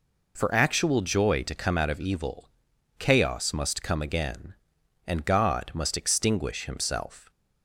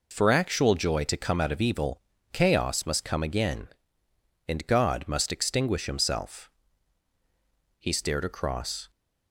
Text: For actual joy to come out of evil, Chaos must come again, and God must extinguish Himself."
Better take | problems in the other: first | goes on to say "He stared across"; noticeable; from 7.7 s on; 1.1 s long

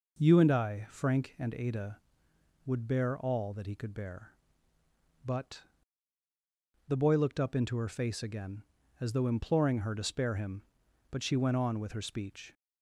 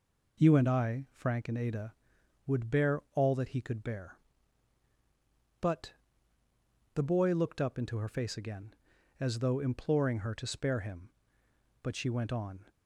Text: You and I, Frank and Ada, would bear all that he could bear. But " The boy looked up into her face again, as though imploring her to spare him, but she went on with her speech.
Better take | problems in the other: first | stops before "with her speech"; at 12.6 s

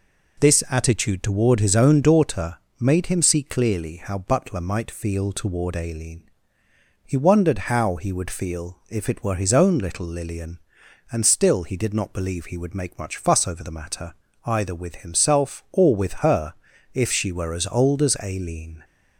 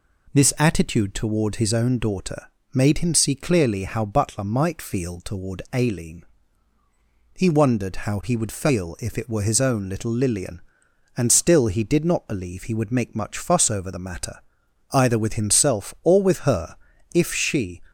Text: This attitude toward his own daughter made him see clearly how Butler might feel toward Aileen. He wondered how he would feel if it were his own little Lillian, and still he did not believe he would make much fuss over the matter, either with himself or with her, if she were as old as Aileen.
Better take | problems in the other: first | pauses between "daughter" and "made"; slight; at 2.4 s; 0.26 s long; slight in the first // stops before "were as old as Aileen"; at 17.8 s

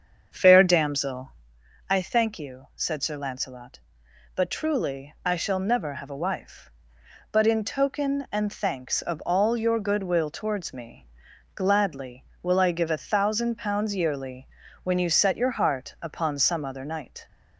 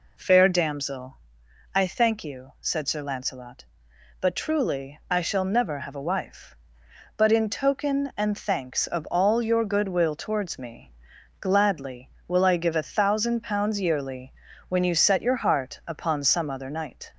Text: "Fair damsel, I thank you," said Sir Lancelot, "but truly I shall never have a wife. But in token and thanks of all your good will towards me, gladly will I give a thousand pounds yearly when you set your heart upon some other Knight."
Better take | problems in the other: second | starts louder than the rest; until 1.6 s; 7 dB // pauses between "yearly" and "when"; slight; at 14.4 s; 0.36 s long; slight in the second

